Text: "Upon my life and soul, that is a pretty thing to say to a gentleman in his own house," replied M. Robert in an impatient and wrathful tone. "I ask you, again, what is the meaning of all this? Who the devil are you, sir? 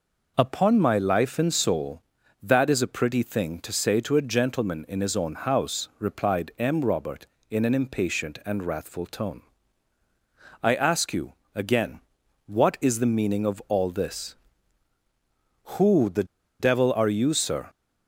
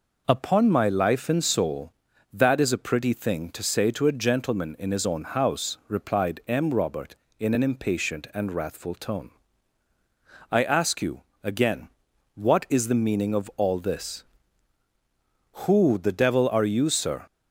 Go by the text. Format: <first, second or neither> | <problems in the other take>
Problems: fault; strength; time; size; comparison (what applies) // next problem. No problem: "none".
second | pauses between "the" and "devil"; slight; at 16.2 s; 0.35 s long